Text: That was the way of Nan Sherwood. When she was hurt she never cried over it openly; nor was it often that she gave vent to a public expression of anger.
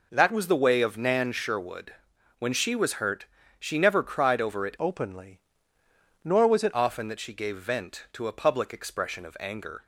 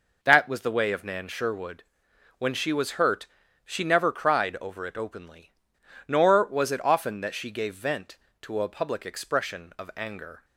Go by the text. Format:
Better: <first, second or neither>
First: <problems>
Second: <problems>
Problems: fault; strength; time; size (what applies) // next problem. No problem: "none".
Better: second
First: pauses between "hurt" and "she"; slight; at 3.2 s; 0.34 s long // changes voice from "openly" to "it"; from 4.7 to 6.7 s; 2.0 s long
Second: pauses between "hurt" and "she"; at 3.2 s; 0.38 s long